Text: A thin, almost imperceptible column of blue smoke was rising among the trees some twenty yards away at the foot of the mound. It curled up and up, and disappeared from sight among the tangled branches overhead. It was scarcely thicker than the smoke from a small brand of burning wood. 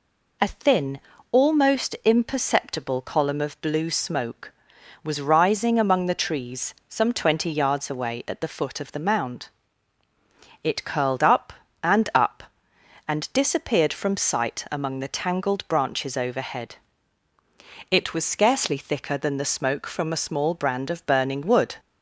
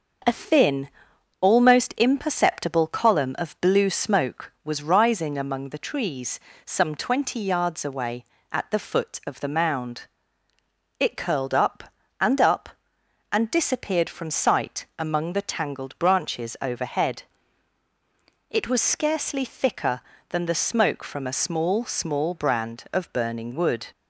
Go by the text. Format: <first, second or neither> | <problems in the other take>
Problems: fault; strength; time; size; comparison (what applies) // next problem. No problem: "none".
first | starts louder than the rest; until 1.7 s; 6.5 dB // pauses between "trees" and "some"; slight; at 6.3 s; 0.26 s long; slight in the first // says "small" twice; at 21.8 s